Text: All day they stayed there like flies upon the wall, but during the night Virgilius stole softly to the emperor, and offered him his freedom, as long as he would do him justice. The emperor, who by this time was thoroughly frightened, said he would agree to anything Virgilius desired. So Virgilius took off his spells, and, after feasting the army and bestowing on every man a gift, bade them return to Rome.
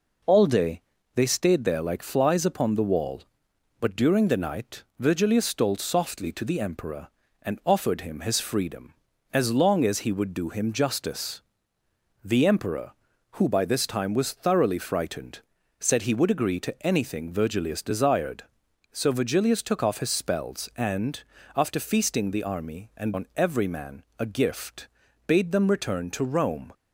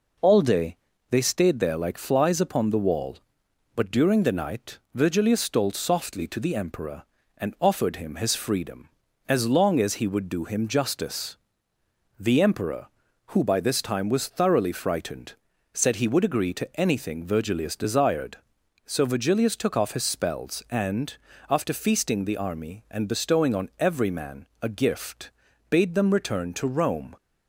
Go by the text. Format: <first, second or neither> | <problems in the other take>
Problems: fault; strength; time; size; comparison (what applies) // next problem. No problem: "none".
second | pauses between "day" and "they"; slight; at 0.8 s; 0.36 s long; slight in the second // skips "bestowing"; at 23.1 s // pauses between "man" and "a"; slight; at 24.0 s; 0.16 s long; slight in the second